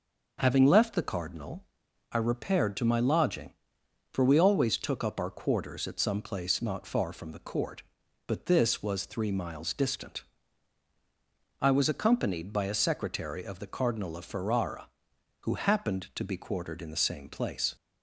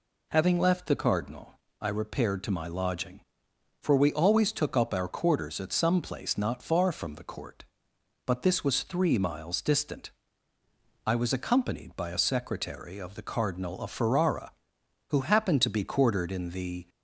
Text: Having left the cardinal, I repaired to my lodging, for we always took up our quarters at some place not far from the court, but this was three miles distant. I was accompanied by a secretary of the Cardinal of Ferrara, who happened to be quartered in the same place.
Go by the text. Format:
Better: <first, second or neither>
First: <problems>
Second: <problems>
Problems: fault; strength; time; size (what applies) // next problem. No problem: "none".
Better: first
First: none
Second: stops before "same place"; at 16.8 s